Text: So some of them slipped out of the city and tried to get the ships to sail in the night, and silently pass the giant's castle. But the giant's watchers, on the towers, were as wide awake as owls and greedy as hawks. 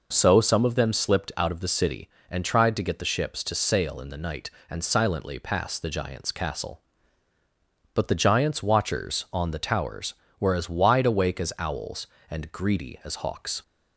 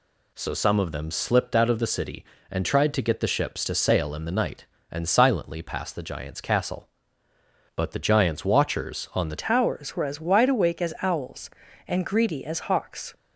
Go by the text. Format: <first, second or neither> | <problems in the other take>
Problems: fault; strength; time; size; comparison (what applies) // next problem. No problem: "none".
first | changes voice at "towers"; from 9.4 s on; 3.7 s long